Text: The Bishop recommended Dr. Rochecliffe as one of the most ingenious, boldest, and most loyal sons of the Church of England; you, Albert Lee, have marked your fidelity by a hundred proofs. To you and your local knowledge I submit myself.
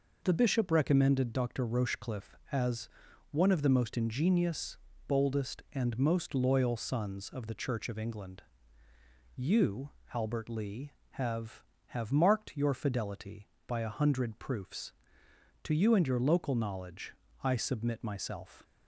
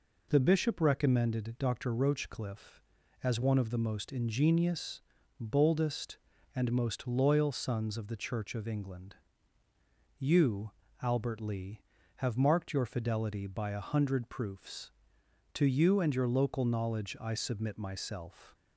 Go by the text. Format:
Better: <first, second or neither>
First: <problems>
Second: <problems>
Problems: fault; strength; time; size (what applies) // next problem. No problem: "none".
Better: second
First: pauses between "as" and "one"; at 2.8 s; 0.44 s long // says "have" twice; at 11.8 s // pauses between "knowledge" and "I"; slight; at 17.1 s; 0.28 s long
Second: none